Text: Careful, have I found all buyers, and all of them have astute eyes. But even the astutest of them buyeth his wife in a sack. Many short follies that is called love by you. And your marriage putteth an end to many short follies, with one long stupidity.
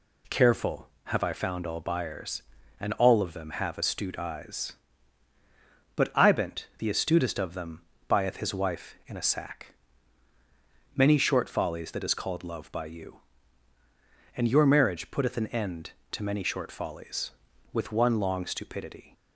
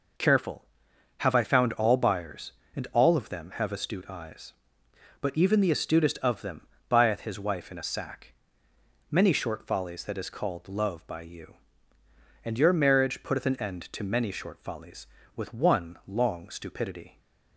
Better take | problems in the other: second | says "ibent" for "even"; at 6.1 s // pauses between "them" and "buyeth"; slight; at 7.8 s; 0.26 s long; slight in the second

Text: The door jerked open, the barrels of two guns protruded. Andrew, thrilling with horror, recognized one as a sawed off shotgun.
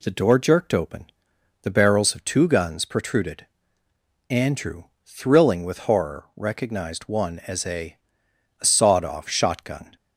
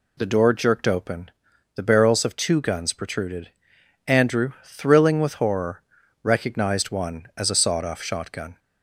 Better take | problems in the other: second | says "a" twice; at 8.5 s

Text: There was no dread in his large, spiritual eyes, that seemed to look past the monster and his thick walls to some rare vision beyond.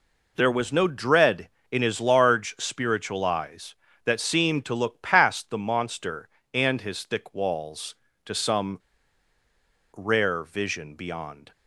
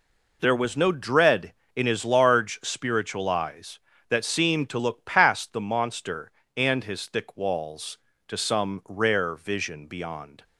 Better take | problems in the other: second | pauses between "some" and "rare"; at 8.7 s; 1.1 s long

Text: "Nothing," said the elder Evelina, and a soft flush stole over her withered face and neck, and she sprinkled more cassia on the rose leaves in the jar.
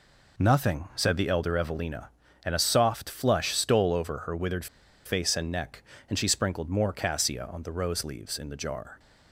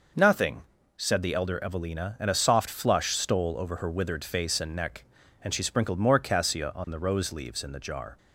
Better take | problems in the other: second | pauses between "withered" and "face"; at 4.6 s; 0.39 s long

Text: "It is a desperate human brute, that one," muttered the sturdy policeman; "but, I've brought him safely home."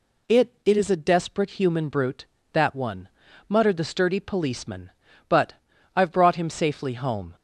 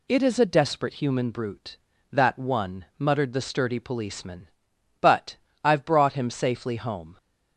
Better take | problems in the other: second | says "It" twice; at 0.6 s

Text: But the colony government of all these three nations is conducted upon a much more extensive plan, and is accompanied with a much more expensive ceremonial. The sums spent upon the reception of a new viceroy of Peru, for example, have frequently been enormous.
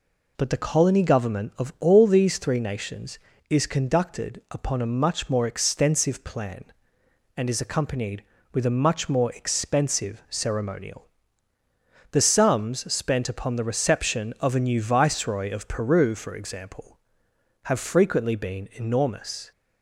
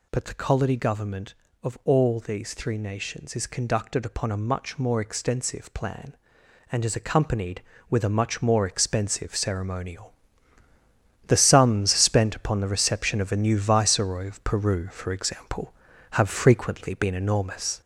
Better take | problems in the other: first | gets louder; noticeable; throughout; 4 dB

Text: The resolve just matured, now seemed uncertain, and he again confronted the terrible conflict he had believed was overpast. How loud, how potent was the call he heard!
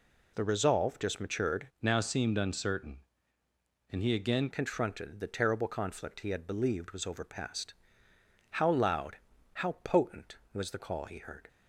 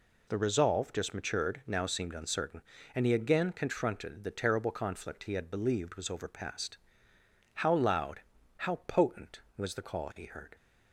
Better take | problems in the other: second | changes voice from "now" to "again"; from 1.8 to 4.4 s; 2.6 s long

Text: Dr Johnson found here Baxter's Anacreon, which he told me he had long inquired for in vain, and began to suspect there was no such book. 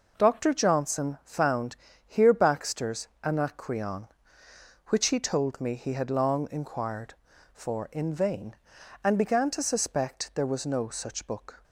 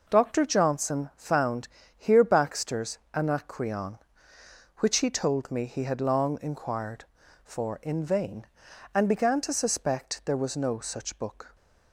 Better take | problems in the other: neither | pauses between "found" and "here"; slight; the same in both // pauses between "Baxter's" and "Anacreon"; slight; the same in both

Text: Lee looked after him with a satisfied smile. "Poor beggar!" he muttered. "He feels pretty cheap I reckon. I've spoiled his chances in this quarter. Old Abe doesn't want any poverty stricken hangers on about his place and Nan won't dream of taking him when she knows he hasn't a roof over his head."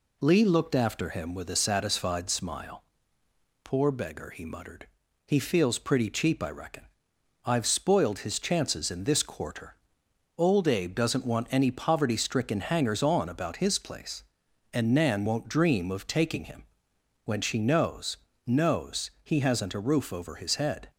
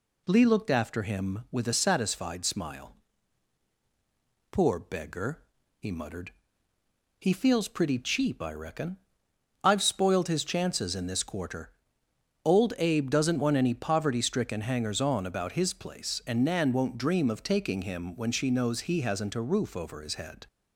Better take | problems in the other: second | pauses between "him" and "when"; noticeable; at 16.6 s; 0.60 s long // says "knows" twice; at 18.4 s

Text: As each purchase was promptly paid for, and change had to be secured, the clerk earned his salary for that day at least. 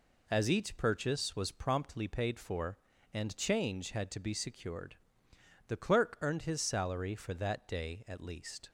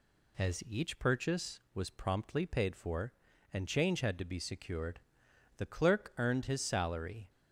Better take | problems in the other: first | stops before "for that day at least"; at 7.2 s

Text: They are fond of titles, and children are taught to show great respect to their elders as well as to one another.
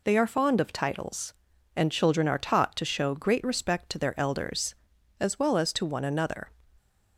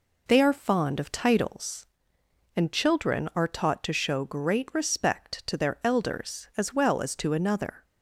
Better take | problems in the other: first | skips "one"; at 7.3 s

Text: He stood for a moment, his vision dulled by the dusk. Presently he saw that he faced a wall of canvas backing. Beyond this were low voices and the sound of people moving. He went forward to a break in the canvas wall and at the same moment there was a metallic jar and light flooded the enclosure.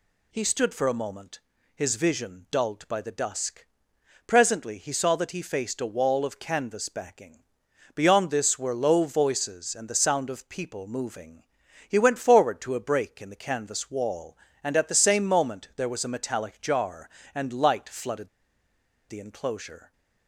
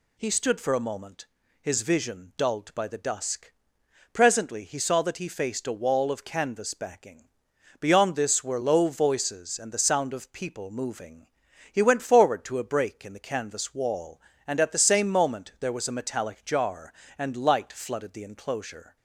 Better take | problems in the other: second | pauses between "flooded" and "the"; noticeable; at 18.2 s; 0.80 s long

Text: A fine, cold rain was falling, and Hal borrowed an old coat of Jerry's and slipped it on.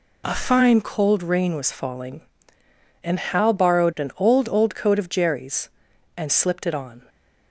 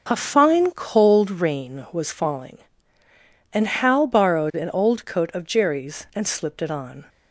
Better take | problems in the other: second | says "old" twice; at 4.4 s

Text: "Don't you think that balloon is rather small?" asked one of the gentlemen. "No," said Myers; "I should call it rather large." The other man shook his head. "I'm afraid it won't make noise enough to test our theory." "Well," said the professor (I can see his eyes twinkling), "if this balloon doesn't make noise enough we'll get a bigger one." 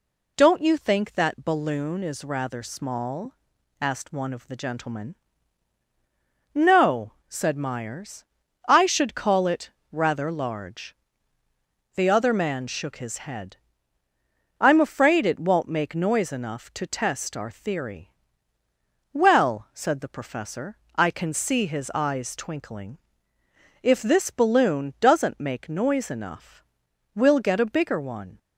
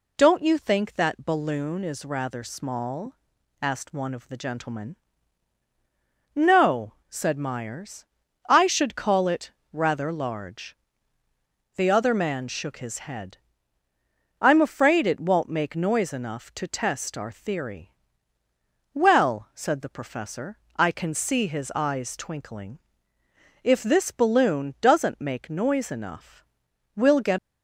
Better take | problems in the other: first | pauses between "it" and "rather"; slight; at 9.5 s; 0.18 s long; slight in the first // pauses between "enough" and "we'll"; noticeable; at 26.4 s; 0.50 s long; noticeable in the first // stops before "a bigger one"; at 27.3 s

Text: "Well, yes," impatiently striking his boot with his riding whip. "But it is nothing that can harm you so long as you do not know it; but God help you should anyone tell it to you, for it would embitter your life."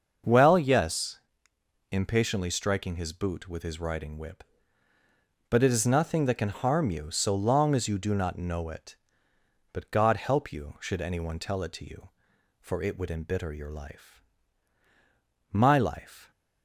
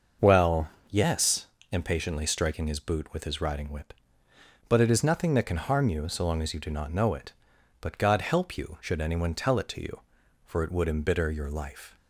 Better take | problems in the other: second | starts louder than the rest; until 1.9 s; 6.5 dB; also in the second // goes on to say "My life"; noticeable; from 15.5 s on; 0.80 s long

